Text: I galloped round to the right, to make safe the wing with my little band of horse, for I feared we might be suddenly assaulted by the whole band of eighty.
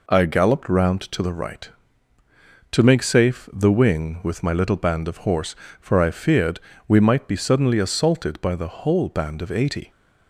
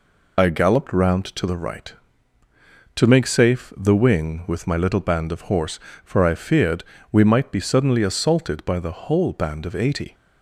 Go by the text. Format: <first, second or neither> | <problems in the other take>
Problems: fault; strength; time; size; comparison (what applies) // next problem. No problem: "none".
first | loses the start of "I"; at 0.3 s; 60 ms // pauses between "feared" and "we"; slight; at 6.8 s; 0.26 s long; slight in the first